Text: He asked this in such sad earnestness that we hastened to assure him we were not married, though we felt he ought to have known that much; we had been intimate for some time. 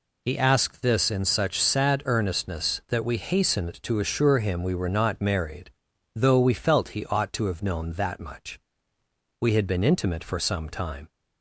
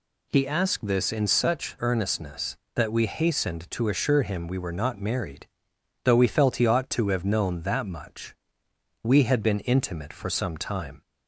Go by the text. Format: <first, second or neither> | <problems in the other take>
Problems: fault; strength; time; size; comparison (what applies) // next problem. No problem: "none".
first | skips "sad"; at 1.7 s